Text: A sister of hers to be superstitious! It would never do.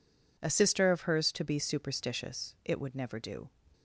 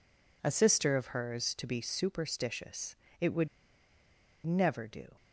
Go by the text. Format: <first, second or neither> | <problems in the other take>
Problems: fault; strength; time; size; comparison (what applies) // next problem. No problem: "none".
first | pauses between "would" and "never"; noticeable; at 3.4 s; 0.97 s long